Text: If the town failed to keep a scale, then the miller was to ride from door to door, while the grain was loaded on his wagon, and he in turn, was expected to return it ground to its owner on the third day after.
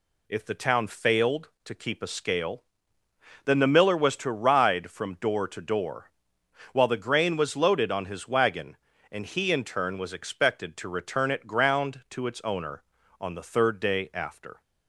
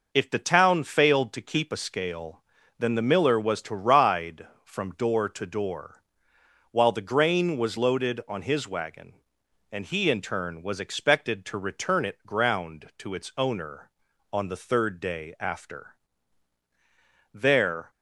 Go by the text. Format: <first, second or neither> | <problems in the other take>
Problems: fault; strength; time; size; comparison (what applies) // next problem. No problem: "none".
first | goes on to say "There"; from 17.3 s on; 0.56 s long